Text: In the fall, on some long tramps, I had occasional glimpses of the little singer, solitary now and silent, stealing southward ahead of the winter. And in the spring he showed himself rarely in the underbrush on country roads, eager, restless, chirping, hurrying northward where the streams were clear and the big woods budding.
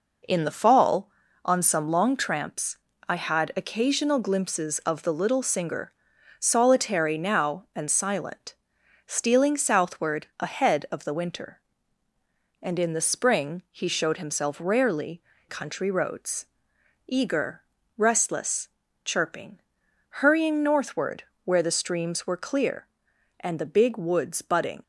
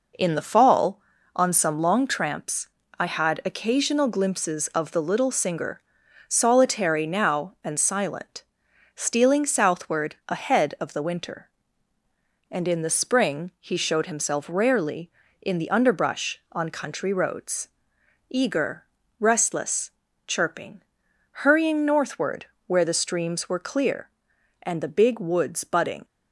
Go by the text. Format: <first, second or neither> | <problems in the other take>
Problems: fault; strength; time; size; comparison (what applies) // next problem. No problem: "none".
second | skips "in the underbrush on"; at 15.3 s // pauses between "northward" and "where"; slight; at 21.2 s; 0.22 s long; slight in the second